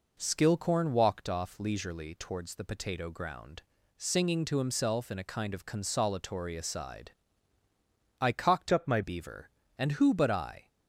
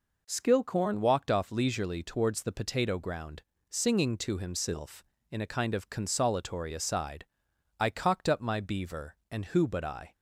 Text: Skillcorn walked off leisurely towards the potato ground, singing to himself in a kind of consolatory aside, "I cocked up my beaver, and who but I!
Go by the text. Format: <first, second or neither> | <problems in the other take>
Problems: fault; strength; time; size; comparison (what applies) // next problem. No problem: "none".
second | changes voice from "up" to "my"; from 8.7 to 9.0 s; 0.3 s long